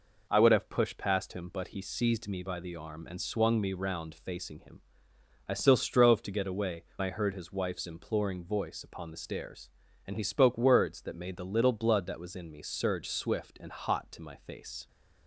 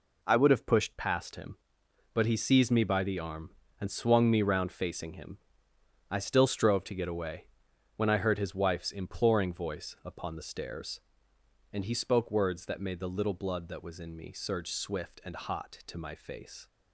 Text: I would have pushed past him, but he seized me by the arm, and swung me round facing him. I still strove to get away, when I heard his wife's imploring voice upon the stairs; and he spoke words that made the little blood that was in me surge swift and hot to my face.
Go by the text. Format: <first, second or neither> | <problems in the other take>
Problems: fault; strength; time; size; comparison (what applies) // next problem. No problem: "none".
second | skips "when"; at 6.9 s